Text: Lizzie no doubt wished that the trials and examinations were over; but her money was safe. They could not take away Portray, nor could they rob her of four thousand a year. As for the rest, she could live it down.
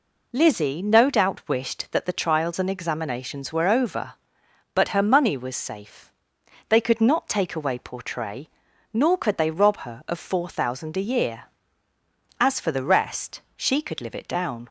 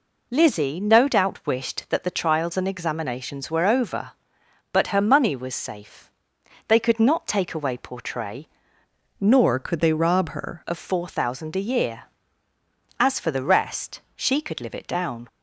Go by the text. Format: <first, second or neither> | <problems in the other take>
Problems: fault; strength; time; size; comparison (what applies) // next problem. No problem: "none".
first | changes voice from "nor" to "her"; from 9.1 to 10.6 s; 1.5 s long